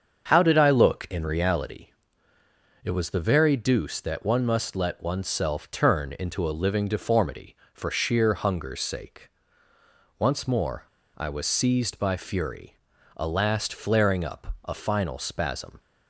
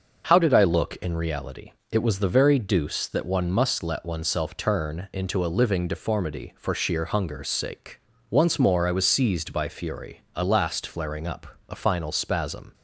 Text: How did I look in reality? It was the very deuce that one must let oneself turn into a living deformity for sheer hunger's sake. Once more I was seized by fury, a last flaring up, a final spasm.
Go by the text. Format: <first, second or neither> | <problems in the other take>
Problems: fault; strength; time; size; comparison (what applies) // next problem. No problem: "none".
second | starts louder than the rest; until 1.2 s; 7 dB; noticeable in the second // pauses between "more" and "I"; slight; at 10.8 s; 0.31 s long